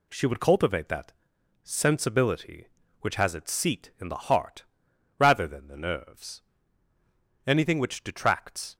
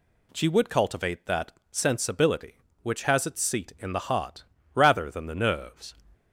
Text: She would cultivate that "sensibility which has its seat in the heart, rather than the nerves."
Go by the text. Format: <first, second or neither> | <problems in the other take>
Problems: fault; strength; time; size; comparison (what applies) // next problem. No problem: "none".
second | pauses between "that" and "sensibility"; noticeable; at 1.1 s; 0.50 s long; slight in the second // goes on to say "Anything which detracts"; noticeable; from 7.4 s on; 1.3 s long